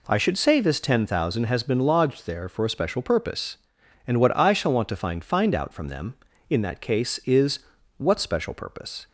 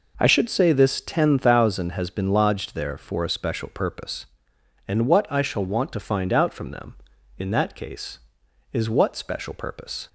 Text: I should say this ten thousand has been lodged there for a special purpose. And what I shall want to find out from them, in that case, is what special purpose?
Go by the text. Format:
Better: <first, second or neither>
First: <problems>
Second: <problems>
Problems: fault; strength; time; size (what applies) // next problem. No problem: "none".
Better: second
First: says "find" twice; at 5.2 s // pauses between "is" and "what"; at 7.5 s; 0.38 s long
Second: none